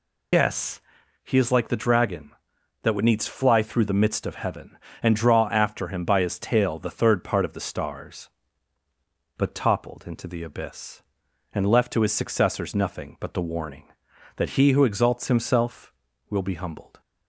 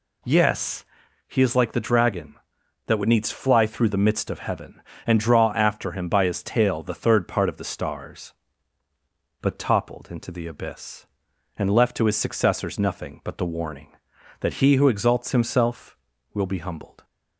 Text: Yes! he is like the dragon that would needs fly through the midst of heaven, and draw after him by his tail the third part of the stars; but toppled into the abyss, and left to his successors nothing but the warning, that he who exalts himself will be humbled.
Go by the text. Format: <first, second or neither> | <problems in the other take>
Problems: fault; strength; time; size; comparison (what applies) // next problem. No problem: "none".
second | loses the start of "Yes"; at 0.3 s; 125 ms